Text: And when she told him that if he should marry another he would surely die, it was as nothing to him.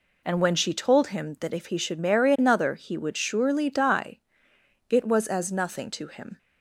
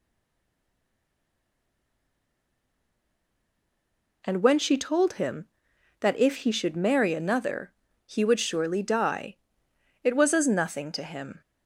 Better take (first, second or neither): first